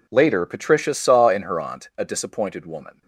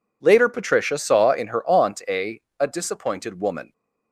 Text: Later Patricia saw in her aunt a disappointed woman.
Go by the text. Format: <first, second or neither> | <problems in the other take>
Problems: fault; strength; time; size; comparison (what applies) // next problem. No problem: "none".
first | says "a" twice; at 2.5 s